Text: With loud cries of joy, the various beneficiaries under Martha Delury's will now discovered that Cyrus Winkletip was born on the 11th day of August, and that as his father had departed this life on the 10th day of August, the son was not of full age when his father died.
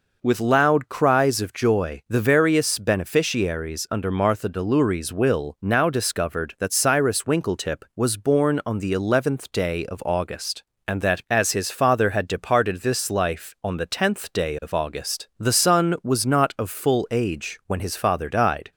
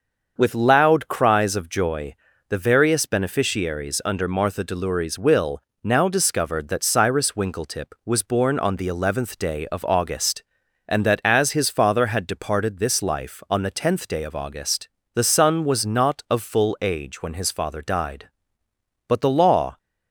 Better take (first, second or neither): first